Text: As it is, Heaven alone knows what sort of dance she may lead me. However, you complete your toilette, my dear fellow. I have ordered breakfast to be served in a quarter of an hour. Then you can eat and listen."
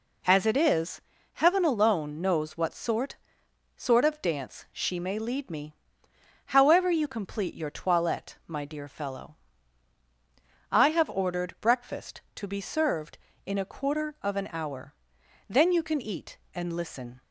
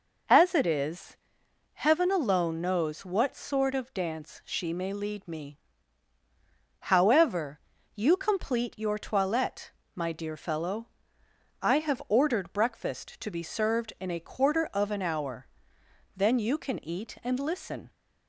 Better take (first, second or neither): second